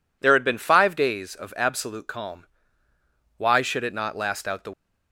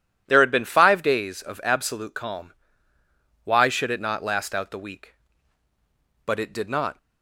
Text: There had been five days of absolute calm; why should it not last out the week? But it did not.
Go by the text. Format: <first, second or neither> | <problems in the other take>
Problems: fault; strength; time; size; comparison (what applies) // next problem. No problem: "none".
second | stops before "week But it did not"; at 4.7 s